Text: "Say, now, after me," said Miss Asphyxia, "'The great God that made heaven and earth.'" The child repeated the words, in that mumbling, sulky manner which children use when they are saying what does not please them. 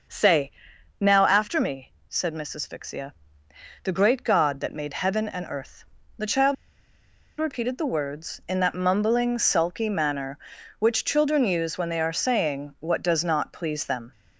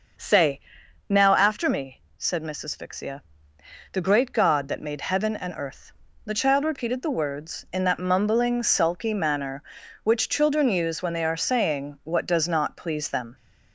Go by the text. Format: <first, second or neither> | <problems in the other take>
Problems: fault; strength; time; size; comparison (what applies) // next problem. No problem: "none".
second | starts louder than the rest; until 1.6 s; 6.5 dB; also in the second // pauses between "child" and "repeated"; noticeable; at 6.5 s; 0.84 s long